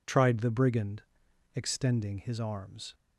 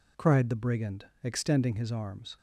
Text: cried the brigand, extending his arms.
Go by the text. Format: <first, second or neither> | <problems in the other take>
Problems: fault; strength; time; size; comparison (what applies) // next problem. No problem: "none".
second | says "tried" for "cried"; at 0.0 s